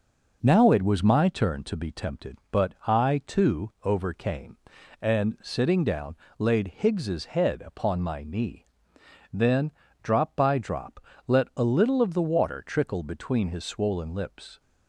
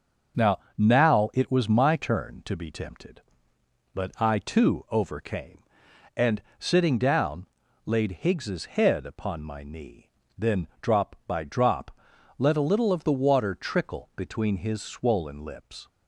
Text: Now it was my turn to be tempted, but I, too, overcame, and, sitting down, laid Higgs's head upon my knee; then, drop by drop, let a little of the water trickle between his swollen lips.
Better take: first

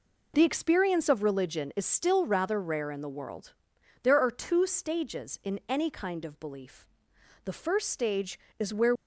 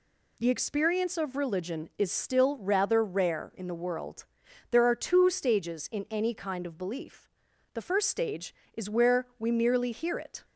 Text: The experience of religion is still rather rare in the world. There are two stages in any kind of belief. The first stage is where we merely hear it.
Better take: second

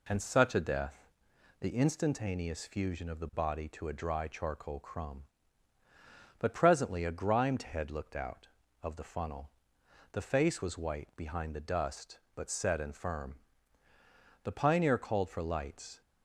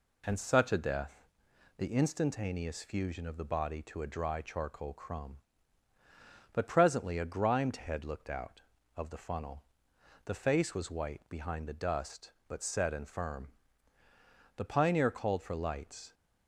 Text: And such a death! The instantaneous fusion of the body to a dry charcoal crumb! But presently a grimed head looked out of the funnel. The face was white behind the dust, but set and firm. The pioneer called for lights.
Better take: neither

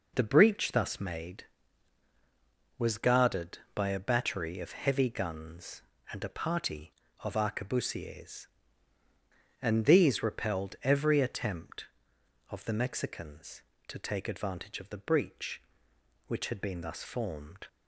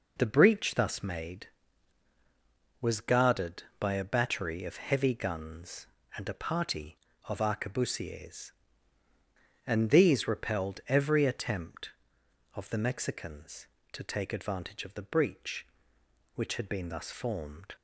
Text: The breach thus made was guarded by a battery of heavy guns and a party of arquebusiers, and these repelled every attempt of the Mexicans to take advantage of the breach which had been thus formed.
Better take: neither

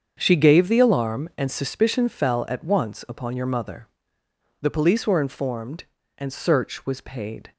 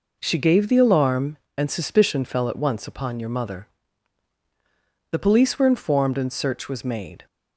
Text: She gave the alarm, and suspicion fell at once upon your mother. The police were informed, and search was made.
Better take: second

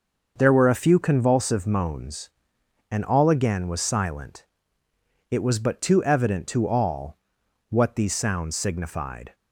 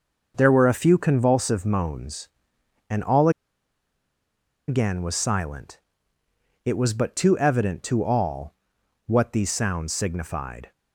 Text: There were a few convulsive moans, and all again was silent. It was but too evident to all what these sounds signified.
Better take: first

